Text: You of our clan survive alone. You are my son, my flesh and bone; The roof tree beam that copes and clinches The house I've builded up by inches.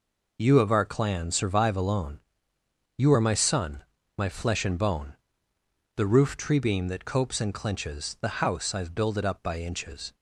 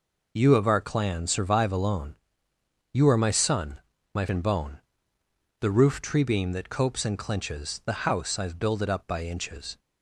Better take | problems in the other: first | skips "flesh"; at 4.2 s

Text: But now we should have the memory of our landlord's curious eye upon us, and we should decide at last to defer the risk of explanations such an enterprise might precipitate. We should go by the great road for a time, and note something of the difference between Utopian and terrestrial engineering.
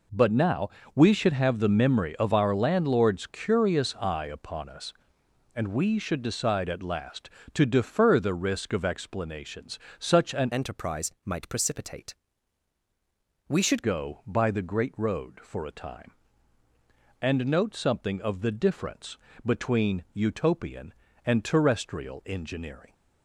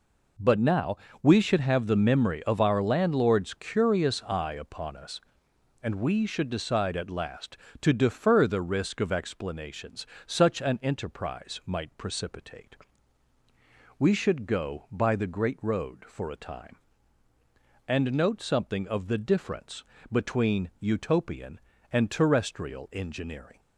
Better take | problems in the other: second | pauses between "now" and "we"; slight; at 0.7 s; 0.24 s long; slight in the second // pauses between "explanations" and "such"; slight; at 9.7 s; 0.20 s long; slight in the second // changes voice from "enterprise" to "should"; from 10.5 to 13.8 s; 3.3 s long // pauses between "difference" and "between"; slight; at 19.1 s; 0.28 s long; slight in the second

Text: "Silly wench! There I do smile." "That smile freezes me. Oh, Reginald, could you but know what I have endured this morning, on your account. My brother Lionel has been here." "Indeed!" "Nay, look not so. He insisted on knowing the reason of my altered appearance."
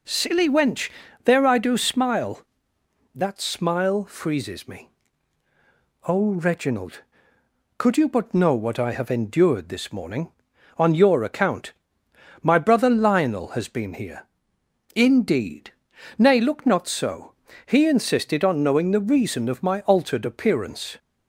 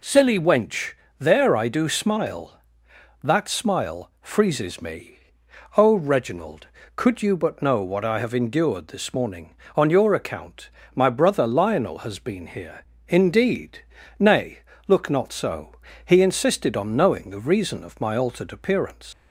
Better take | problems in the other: first | leaves "appearance" unfinished; at 19.1 s; 135 ms

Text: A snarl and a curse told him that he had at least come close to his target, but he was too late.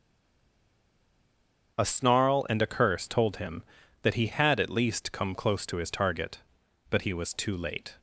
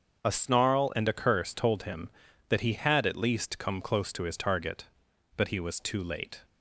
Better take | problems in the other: second | stays silent before the first word; noticeable; until 1.7 s; 1.7 s long // starts louder than the rest; until 2.7 s; 6.5 dB; also in the second

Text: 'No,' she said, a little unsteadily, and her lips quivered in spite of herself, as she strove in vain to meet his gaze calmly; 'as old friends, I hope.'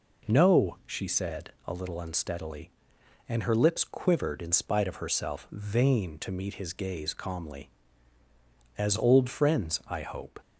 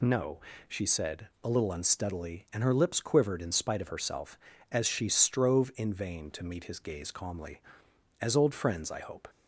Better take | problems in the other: second | skips "as she strove in"; at 5.4 s

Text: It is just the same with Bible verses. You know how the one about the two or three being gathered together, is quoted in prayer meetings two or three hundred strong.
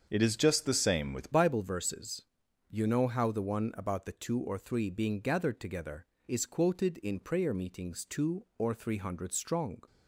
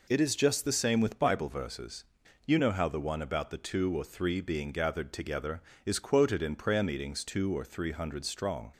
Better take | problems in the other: second | starts louder than the rest; until 1.1 s; 7 dB // changes voice at "Bible"; from 1.3 s on; 8.5 s long

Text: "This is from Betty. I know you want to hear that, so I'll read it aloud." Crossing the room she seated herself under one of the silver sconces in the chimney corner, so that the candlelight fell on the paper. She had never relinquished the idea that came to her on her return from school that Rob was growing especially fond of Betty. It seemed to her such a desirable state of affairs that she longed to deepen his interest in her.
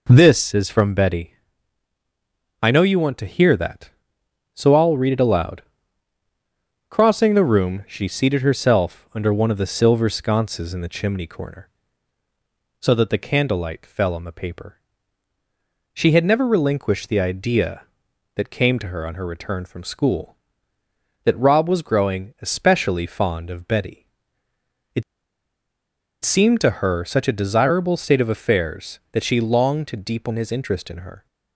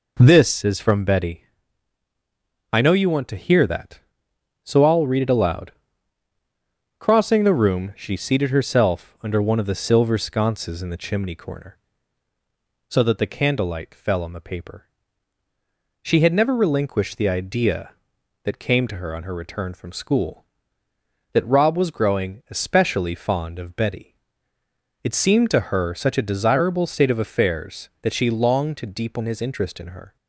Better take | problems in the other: second | pauses between "It" and "seemed"; at 25.0 s; 1.2 s long

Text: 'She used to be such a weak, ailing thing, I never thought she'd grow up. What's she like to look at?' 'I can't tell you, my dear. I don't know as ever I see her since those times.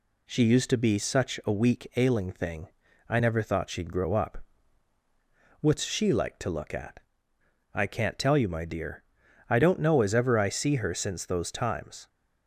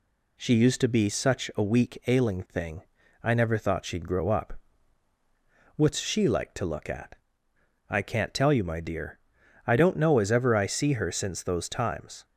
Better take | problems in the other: neither | none

